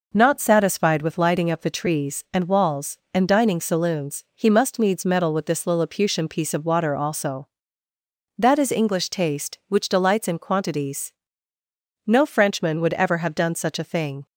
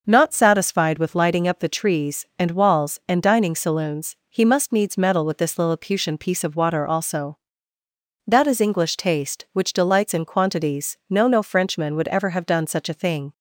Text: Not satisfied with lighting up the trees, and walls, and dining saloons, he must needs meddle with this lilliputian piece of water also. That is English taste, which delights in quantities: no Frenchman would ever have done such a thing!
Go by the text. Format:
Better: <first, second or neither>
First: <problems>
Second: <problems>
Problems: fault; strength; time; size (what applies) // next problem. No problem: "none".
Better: first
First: none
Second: says "no" twice; at 11.2 s